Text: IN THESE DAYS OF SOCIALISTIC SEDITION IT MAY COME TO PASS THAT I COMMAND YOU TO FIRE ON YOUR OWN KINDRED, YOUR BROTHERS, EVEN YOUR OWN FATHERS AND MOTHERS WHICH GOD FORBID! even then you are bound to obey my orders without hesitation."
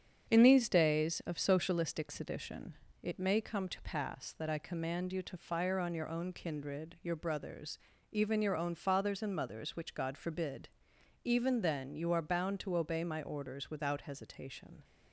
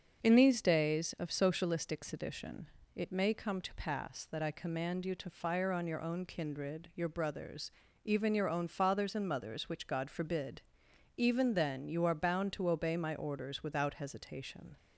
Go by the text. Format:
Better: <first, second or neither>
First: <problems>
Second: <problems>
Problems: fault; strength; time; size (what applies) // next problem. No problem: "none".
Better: second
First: gets quieter; noticeable; throughout; 4.5 dB // starts louder than the rest; strong; until 1.3 s; 7.5 dB // pauses between "SEDITION" and "IT"; slight; at 2.7 s; 0.28 s long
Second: starts louder than the rest; until 1.2 s; 6.5 dB // pauses between "SEDITION" and "IT"; slight; at 2.6 s; 0.28 s long